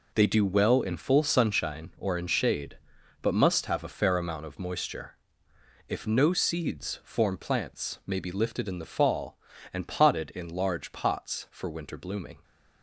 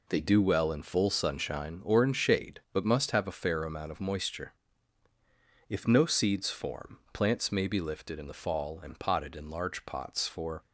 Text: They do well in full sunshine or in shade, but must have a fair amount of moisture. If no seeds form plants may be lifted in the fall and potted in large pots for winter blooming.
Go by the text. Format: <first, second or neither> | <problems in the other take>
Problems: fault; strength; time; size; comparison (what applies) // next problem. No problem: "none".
first | stops before "winter blooming"; at 10.6 s